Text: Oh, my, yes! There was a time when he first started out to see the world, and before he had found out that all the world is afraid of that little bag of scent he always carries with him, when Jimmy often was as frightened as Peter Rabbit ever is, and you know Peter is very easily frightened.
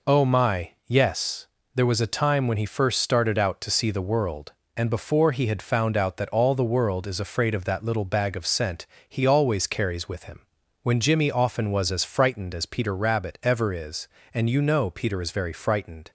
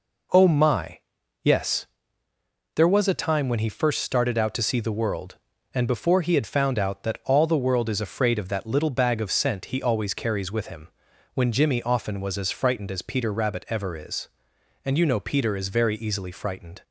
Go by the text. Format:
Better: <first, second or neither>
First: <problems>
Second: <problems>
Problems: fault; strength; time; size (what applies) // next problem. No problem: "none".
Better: second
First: pauses between "scent" and "he"; slight; at 8.8 s; 0.24 s long // skips "easily"; at 15.5 s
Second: none